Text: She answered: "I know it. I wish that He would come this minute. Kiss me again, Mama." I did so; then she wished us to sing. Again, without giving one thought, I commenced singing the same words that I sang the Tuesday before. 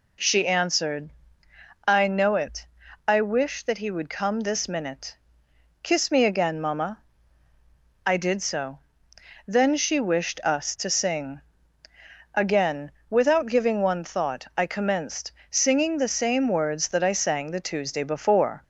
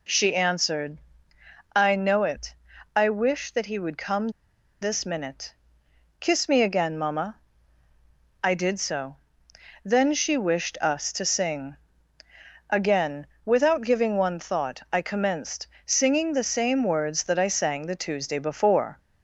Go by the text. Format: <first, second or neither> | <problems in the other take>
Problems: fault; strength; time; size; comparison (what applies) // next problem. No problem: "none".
first | pauses between "come" and "this"; noticeable; at 4.2 s; 0.52 s long // pauses between "commenced" and "singing"; slight; at 15.6 s; 0.18 s long; slight in the first